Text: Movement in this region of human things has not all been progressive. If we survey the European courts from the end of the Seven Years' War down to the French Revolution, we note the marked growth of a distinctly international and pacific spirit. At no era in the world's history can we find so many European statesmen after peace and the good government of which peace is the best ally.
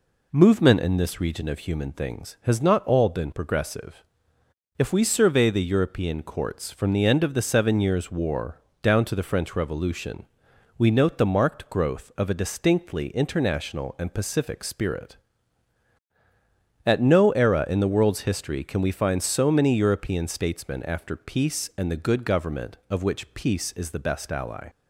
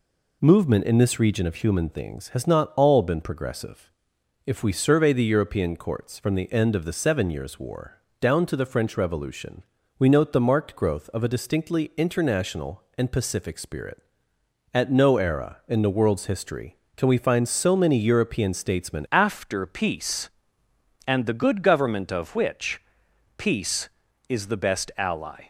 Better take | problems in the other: first | pauses between "War" and "down"; slight; at 7.9 s; 0.22 s long; slight in the first // changes voice at "after"; from 19.1 s on; 6.3 s long // pauses between "which" and "peace"; noticeable; at 22.7 s; 0.56 s long

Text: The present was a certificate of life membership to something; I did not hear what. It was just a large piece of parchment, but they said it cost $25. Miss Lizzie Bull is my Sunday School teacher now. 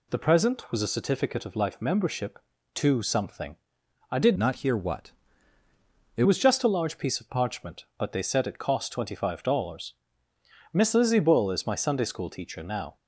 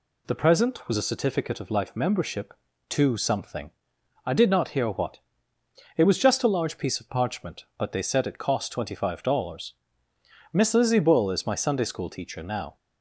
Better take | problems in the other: second | changes voice from "not" to "It"; from 4.3 to 6.2 s; 1.9 s long

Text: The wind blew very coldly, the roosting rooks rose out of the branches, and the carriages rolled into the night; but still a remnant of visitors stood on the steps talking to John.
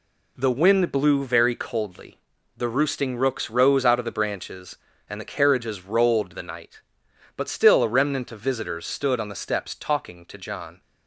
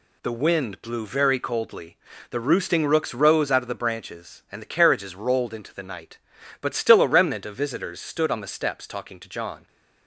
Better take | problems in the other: second | skips "into"; at 6.3 s

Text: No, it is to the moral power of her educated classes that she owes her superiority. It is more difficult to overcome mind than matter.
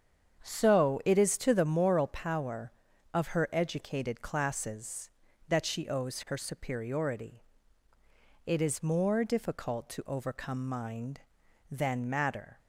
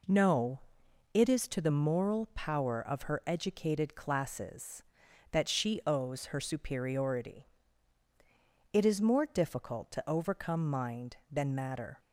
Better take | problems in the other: second | starts louder than the rest; strong; until 1.4 s; 7.5 dB // says "So" for "No"; at 0.4 s

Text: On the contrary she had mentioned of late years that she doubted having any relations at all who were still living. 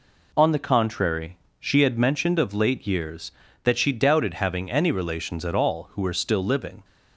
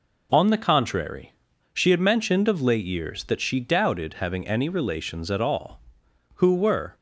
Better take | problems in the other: first | pauses between "contrary" and "she"; at 1.3 s; 0.40 s long; slight in the first // stops before "still living"; at 6.9 s

